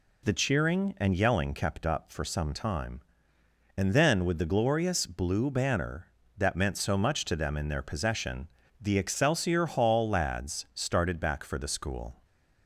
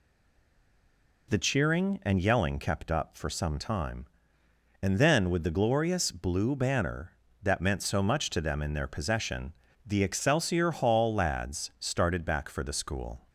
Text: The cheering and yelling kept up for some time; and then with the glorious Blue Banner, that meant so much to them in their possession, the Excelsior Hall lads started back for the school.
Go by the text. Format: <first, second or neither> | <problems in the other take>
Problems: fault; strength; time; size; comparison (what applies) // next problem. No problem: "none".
first | stays silent before the first word; noticeable; until 1.2 s; 1.2 s long